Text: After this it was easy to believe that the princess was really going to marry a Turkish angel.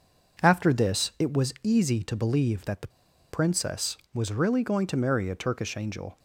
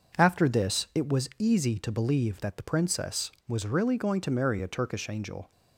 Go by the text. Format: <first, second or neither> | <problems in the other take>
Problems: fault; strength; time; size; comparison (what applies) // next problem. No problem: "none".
second | pauses between "the" and "princess"; at 2.8 s; 0.43 s long